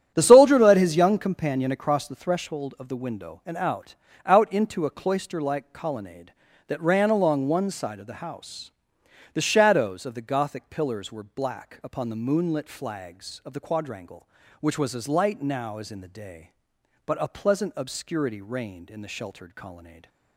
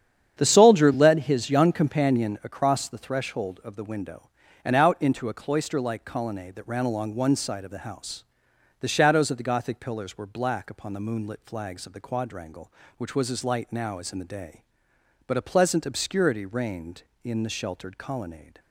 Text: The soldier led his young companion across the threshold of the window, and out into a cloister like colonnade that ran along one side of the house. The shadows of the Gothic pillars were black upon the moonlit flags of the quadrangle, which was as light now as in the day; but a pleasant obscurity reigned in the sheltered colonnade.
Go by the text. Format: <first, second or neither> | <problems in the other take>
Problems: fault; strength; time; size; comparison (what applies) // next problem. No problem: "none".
second | starts louder than the rest; strong; until 1.1 s; 10 dB; strong in the second // says "out" twice; at 4.2 s // stays silent after the last word; slight; from 19.8 s on; 0.5 s long